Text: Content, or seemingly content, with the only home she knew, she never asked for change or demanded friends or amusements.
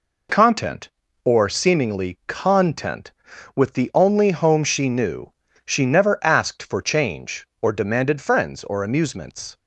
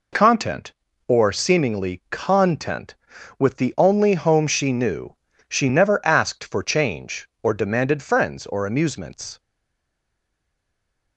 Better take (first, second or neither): first